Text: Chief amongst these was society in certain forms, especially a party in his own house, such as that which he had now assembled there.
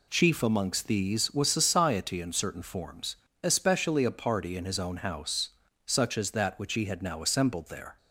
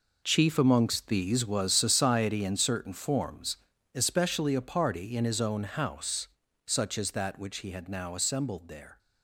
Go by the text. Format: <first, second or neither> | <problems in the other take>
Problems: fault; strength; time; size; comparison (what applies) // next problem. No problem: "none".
first | gets quieter; strong; throughout; 11.5 dB